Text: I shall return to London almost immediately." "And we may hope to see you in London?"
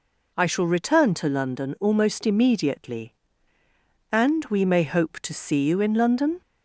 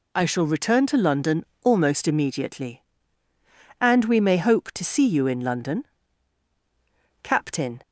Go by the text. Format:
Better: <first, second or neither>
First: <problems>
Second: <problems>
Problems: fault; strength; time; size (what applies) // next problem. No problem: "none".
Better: first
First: none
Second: pauses between "London" and "almost"; slight; at 1.4 s; 0.18 s long // goes on to say "Captain"; from 7.2 s on; 0.60 s long